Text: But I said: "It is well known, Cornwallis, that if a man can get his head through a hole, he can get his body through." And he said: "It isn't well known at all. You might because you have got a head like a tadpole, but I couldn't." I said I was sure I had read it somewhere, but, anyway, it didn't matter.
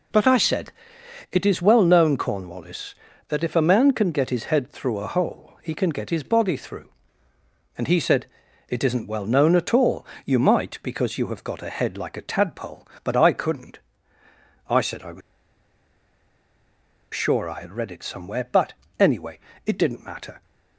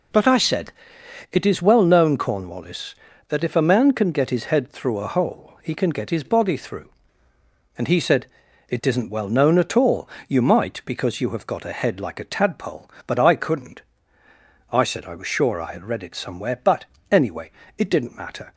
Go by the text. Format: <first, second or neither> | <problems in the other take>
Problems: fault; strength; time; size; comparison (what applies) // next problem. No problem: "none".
second | pauses between "was" and "sure"; strong; at 15.2 s; 1.9 s long